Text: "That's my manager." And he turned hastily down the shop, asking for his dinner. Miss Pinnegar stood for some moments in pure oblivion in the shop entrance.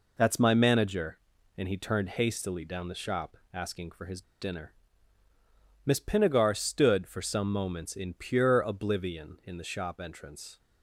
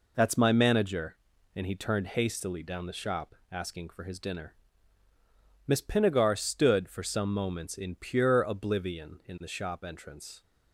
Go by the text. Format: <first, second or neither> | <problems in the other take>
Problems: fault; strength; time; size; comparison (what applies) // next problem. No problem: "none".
second | pauses between "his" and "dinner"; slight; at 4.2 s; 0.19 s long